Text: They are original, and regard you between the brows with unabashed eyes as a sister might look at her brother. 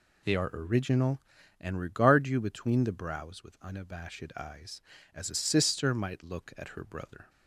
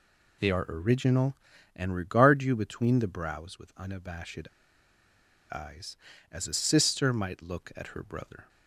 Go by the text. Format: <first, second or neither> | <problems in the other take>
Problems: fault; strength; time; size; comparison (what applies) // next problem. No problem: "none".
first | pauses between "unabashed" and "eyes"; at 4.4 s; 1.0 s long